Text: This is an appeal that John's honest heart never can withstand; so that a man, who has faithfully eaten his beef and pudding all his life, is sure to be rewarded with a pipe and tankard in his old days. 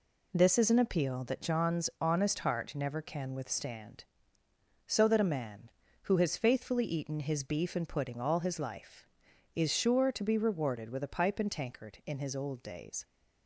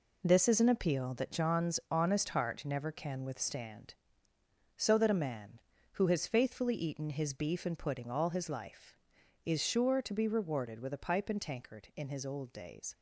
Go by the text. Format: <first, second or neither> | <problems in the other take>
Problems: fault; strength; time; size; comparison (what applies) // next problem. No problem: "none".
first | gets quieter; strong; throughout; 8 dB